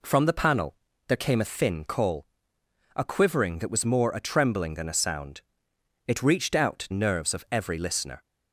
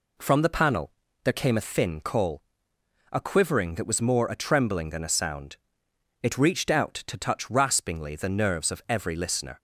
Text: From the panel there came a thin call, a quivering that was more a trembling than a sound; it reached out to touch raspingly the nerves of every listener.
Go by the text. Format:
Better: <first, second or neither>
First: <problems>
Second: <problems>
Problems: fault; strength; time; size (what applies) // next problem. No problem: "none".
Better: second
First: pauses between "panel" and "there"; slight; at 0.7 s; 0.32 s long // skips "to touch raspingly the"; at 6.8 s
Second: pauses between "panel" and "there"; slight; at 0.9 s; 0.32 s long